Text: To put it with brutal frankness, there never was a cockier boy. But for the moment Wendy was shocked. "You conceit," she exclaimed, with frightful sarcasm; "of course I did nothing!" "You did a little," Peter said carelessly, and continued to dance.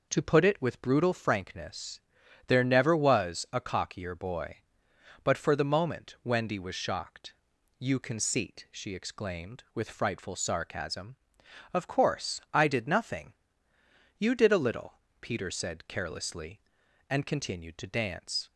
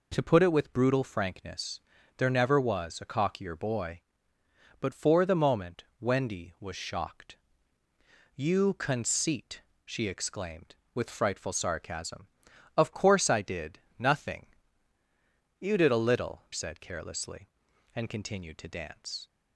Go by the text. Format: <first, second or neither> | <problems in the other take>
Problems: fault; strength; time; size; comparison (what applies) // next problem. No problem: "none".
first | pauses between "moment" and "Wendy"; slight; at 5.8 s; 0.16 s long // pauses between "did" and "nothing"; slight; at 13.7 s; 0.18 s long // skips "Peter"; at 16.4 s